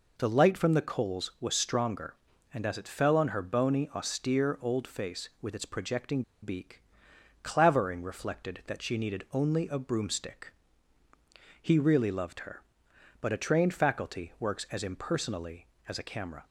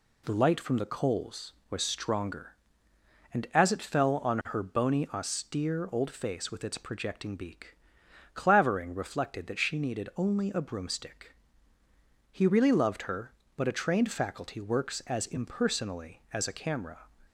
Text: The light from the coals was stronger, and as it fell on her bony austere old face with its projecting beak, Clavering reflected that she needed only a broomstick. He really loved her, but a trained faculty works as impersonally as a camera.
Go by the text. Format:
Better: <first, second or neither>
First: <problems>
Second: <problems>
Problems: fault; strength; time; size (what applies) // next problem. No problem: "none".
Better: second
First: pauses between "projecting" and "beak"; slight; at 6.2 s; 0.20 s long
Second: none